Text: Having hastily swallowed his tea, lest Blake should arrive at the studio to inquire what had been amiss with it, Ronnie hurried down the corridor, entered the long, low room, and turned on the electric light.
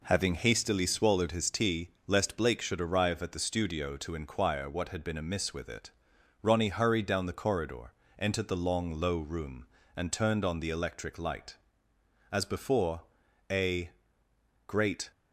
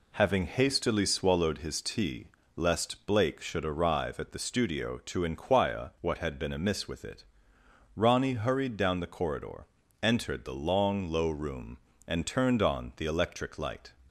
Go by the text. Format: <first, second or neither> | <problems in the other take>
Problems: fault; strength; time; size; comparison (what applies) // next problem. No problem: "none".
second | goes on to say "As before a great"; strong; from 12.3 s on; 2.7 s long